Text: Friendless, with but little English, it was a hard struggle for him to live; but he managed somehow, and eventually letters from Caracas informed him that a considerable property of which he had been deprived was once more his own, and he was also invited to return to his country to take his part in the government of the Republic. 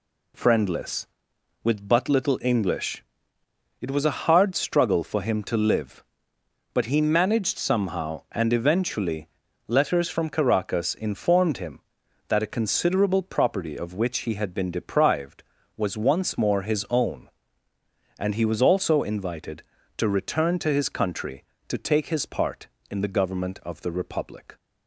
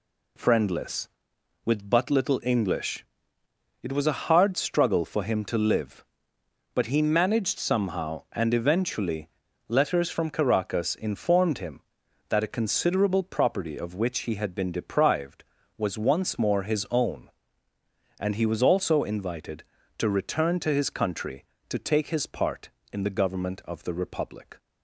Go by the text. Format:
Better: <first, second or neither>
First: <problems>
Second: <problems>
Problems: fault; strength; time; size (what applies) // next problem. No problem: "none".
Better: neither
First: pauses between "eventually" and "letters"; slight; at 9.2 s; 0.36 s long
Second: pauses between "eventually" and "letters"; slight; at 9.3 s; 0.36 s long